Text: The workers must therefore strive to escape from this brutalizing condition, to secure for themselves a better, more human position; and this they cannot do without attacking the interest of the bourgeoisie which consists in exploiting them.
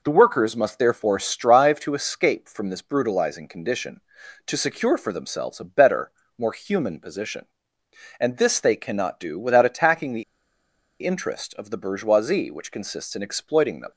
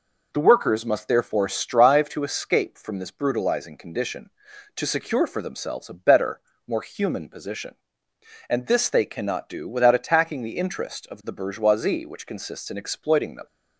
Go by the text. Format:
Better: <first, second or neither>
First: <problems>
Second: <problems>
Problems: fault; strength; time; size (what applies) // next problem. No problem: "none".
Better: second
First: pauses between "the" and "interest"; noticeable; at 10.2 s; 0.79 s long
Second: none